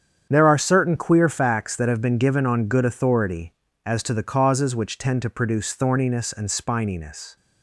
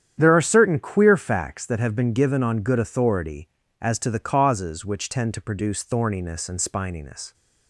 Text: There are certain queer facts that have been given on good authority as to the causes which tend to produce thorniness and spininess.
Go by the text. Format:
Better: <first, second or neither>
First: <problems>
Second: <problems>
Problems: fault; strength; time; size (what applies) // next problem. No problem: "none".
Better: neither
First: starts louder than the rest; strong; until 1.3 s; 8.5 dB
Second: starts louder than the rest; strong; until 1.1 s; 9.5 dB